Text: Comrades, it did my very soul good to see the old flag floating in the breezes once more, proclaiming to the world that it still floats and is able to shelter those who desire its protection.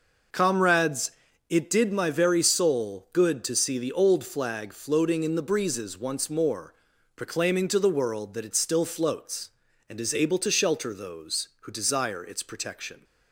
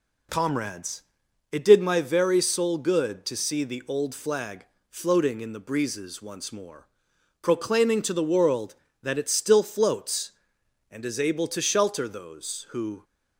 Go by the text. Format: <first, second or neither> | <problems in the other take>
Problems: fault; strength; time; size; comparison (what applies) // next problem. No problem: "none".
first | pauses between "flag" and "floating"; slight; at 4.6 s; 0.22 s long // stops before "desire its protection"; at 13.0 s